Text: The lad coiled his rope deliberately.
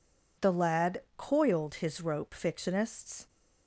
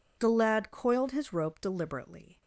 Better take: second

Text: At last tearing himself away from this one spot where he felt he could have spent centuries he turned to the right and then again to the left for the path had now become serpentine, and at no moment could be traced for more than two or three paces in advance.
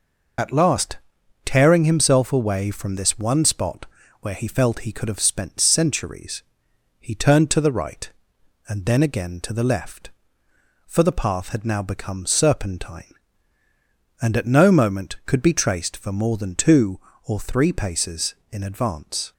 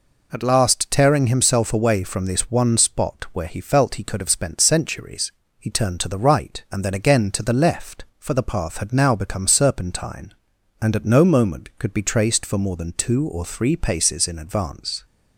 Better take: second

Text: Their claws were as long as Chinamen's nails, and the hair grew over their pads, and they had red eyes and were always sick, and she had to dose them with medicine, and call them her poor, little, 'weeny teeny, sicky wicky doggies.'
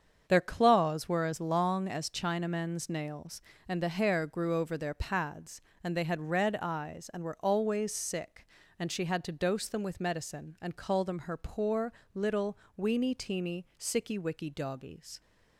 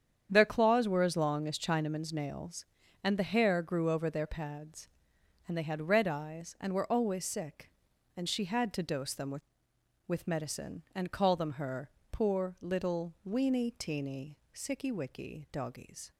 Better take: first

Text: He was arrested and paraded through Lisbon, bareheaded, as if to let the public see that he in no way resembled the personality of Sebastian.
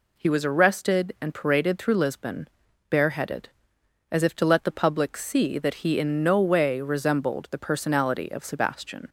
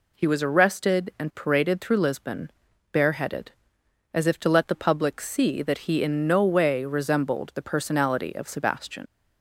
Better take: first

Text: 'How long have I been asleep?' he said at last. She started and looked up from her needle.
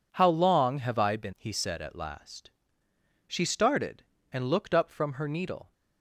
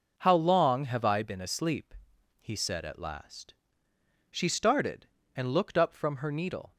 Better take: second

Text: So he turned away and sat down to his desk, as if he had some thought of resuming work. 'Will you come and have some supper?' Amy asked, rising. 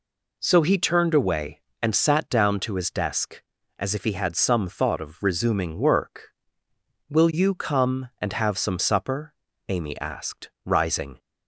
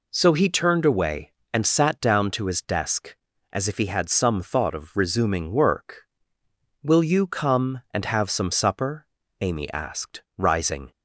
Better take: neither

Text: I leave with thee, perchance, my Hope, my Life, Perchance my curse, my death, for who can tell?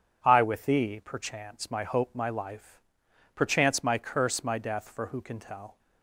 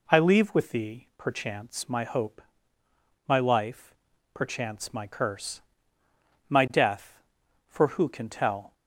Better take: second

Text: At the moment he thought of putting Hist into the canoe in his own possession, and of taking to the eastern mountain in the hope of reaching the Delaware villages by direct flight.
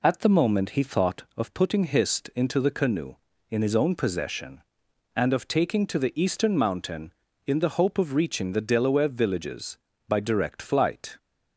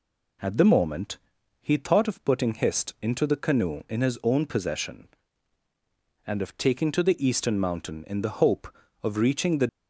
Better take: first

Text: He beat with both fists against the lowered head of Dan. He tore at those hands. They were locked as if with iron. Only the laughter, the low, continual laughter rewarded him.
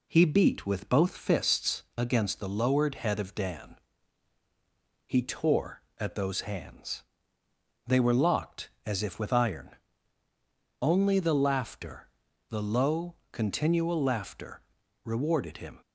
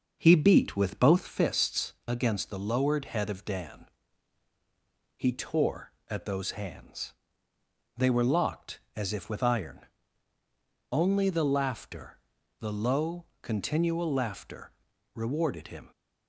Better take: first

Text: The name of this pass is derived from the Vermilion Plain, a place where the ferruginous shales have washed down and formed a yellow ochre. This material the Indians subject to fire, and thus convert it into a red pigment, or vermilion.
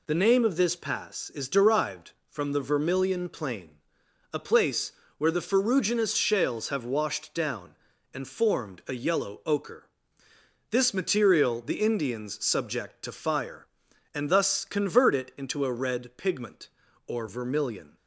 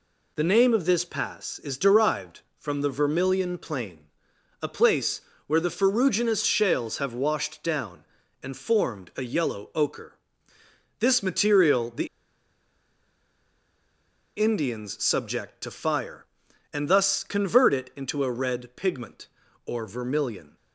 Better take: first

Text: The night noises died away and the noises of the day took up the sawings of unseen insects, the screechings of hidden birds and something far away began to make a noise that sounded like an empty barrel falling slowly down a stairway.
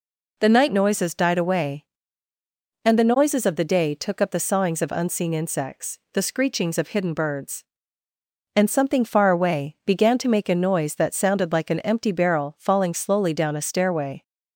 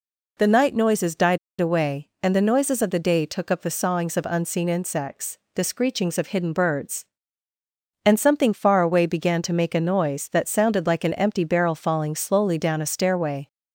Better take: first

